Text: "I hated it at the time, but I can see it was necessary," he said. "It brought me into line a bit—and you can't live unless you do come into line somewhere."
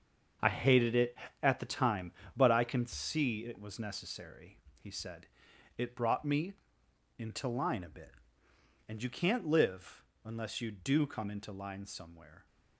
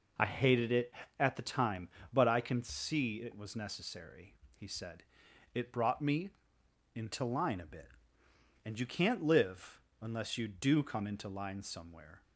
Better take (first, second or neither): second